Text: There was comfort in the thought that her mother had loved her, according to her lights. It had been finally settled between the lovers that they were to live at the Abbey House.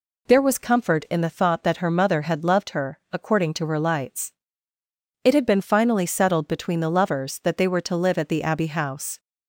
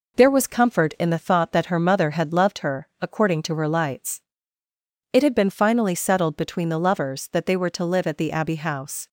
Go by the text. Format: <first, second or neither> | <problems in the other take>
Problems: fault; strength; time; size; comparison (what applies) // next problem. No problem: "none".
first | gets quieter; slight; throughout; 3 dB